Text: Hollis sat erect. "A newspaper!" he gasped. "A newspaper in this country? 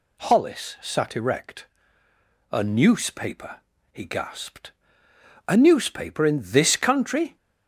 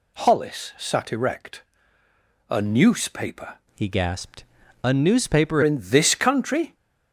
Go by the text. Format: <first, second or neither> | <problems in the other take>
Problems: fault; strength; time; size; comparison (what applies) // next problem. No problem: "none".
first | changes voice from "he" to "newspaper"; from 3.7 to 5.6 s; 1.9 s long